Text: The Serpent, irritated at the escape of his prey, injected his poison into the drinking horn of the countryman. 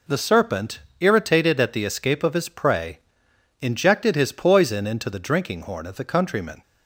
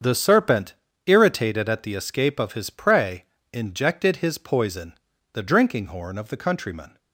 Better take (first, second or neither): first